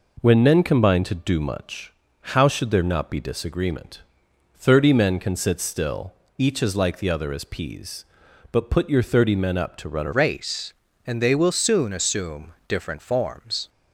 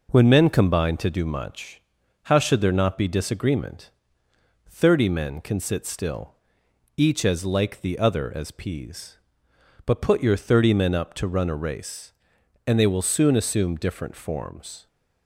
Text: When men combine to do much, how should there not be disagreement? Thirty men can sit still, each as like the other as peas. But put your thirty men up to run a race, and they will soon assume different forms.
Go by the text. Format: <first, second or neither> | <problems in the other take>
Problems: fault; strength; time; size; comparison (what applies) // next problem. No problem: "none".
second | changes voice at "race"; from 10.1 s on; 3.5 s long